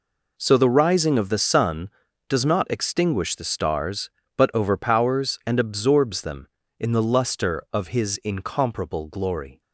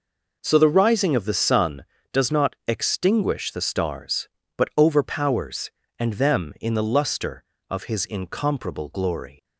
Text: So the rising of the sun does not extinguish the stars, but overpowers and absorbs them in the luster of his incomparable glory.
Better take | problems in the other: first | skips "absorbs"; at 6.1 s

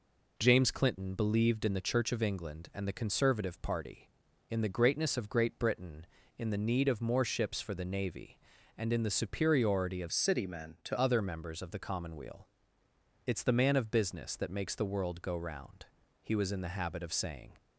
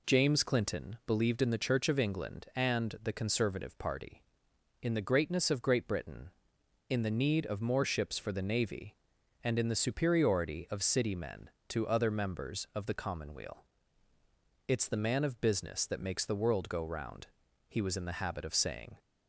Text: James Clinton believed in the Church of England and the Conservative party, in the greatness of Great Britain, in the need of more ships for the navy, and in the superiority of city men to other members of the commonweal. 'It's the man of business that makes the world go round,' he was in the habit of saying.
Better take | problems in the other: second | changes voice from "city" to "to"; from 10.1 to 10.9 s; 0.8 s long

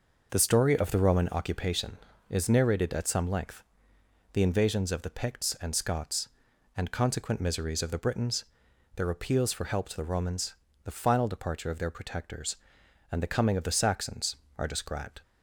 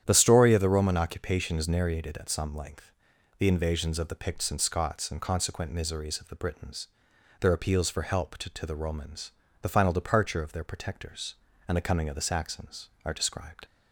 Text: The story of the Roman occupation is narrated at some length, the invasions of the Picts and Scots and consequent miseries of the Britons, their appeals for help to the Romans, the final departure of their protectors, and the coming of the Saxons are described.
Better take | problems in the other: first | starts louder than the rest; strong; until 1.0 s; 10 dB // says "to" twice; at 8.5 s

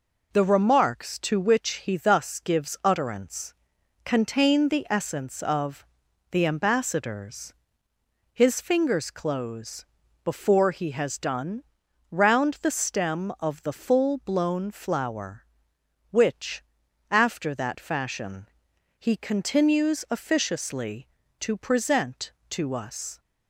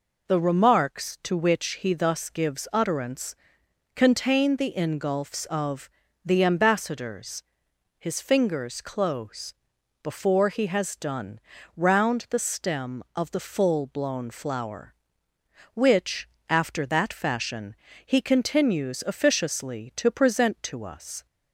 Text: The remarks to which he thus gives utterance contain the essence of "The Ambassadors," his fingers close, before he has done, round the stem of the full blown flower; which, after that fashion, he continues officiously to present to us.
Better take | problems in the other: first | pauses between "utterance" and "contain"; noticeable; at 3.3 s; 0.58 s long; noticeable in the first // says "ingulfs" for "essence"; at 4.7 s // pauses between "of" and "The"; slight; at 5.8 s; 0.34 s long; also in the first

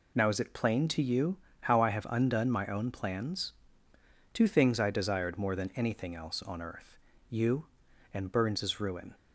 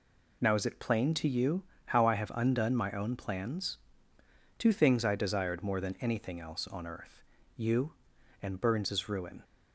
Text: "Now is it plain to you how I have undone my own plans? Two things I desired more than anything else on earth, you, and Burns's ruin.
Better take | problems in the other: neither | pauses between "you" and "how"; slight; the same in both

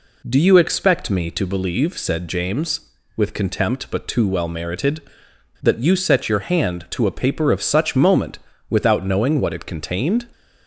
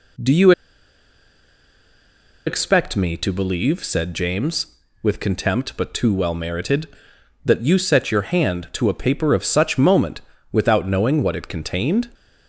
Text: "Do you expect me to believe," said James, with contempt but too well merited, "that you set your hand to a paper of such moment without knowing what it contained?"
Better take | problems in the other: first | pauses between "you" and "expect"; strong; at 0.5 s; 1.9 s long // pauses between "moment" and "without"; slight; at 10.2 s; 0.30 s long; slight in the first

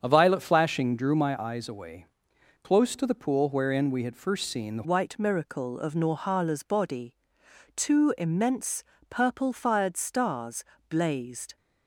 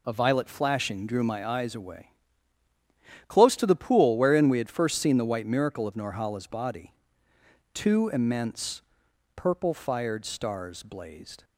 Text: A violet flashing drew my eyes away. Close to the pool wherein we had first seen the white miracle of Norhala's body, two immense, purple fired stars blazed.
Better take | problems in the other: second | starts louder than the rest; strong; until 1.0 s; 7.5 dB // changes voice at "white"; from 4.8 s on; 6.7 s long // pauses between "stars" and "blazed"; slight; at 10.6 s; 0.26 s long

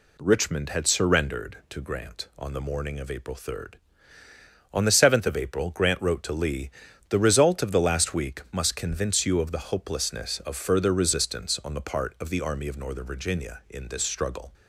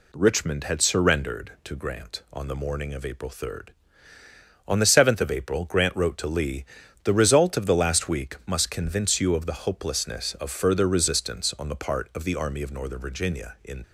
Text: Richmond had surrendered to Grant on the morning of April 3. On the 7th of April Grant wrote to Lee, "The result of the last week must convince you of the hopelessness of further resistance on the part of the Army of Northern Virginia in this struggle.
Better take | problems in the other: first | stops before "this struggle"; at 13.8 s

